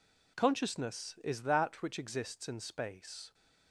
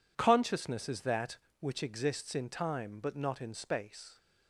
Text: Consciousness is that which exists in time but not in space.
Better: second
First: skips "in time but not"; at 2.4 s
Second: none

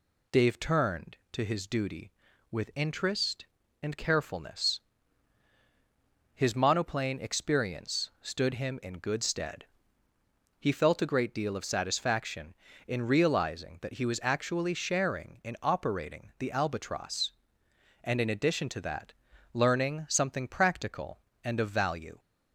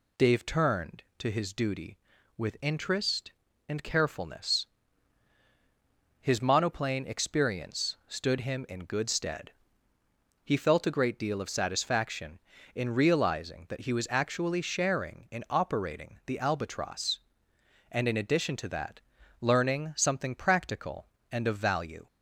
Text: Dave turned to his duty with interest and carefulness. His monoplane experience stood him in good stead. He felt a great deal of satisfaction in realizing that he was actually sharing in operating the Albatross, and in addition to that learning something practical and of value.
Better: neither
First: pauses between "that" and "learning"; at 19.1 s; 0.40 s long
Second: pauses between "that" and "learning"; at 19.0 s; 0.40 s long

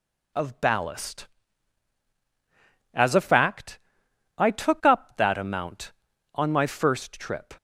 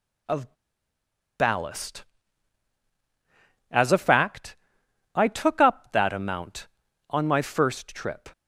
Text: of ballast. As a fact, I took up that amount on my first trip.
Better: first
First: none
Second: pauses between "of" and "ballast"; noticeable; at 0.5 s; 0.87 s long

